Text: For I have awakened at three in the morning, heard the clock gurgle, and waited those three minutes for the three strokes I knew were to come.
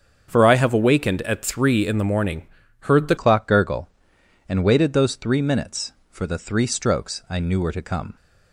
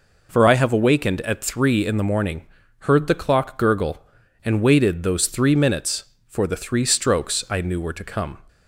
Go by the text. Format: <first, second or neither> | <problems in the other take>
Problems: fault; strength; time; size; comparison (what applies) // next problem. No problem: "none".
second | starts louder than the rest; strong; until 1.3 s; 7 dB // changes voice at "clock"; from 3.1 s on; 5.0 s long